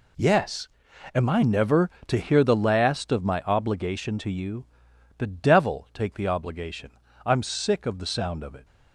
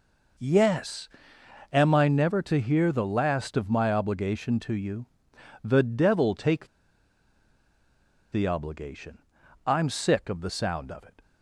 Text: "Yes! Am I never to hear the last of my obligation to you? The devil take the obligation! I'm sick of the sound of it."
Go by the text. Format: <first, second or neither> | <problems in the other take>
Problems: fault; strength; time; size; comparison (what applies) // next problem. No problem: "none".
first | pauses between "take" and "the"; strong; at 6.6 s; 1.6 s long